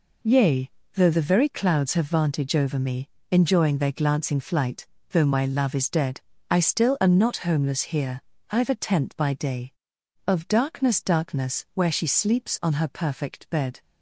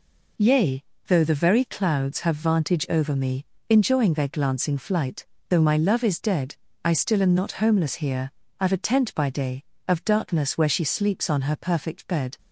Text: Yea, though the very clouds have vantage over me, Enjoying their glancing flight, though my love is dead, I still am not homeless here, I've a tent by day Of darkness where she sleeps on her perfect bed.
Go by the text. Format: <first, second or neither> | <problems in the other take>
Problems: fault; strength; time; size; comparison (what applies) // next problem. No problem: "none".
second | says "darkness" twice; at 10.9 s